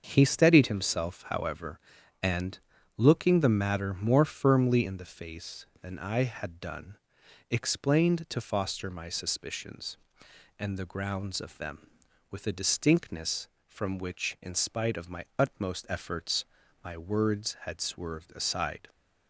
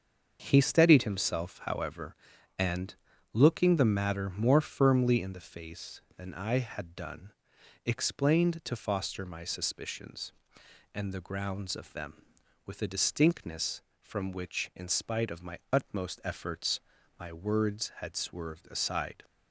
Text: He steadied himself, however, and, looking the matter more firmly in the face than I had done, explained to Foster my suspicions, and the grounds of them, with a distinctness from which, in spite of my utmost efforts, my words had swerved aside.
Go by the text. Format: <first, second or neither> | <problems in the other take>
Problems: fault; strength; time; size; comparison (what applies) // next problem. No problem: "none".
neither | starts louder than the rest; the same in both